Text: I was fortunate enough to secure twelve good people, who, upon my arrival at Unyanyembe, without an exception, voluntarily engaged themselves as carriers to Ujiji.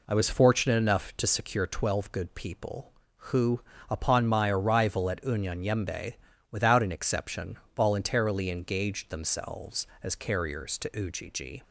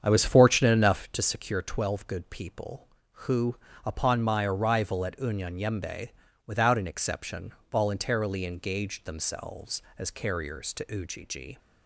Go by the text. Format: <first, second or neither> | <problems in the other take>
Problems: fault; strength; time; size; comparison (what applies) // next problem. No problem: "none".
first | starts louder than the rest; strong; until 1.1 s; 7.5 dB